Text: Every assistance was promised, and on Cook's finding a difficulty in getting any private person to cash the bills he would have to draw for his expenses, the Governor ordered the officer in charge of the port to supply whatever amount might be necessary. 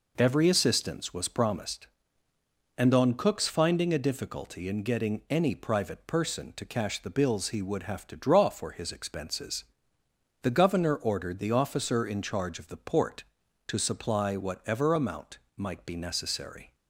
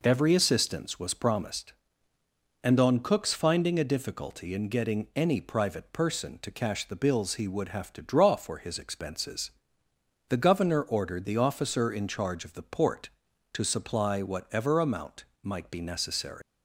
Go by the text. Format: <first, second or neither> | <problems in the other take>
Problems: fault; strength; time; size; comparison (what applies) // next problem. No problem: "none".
first | pauses between "amount" and "might"; slight; at 15.2 s; 0.18 s long; slight in the first // leaves "necessary" unfinished; at 16.4 s; 180 ms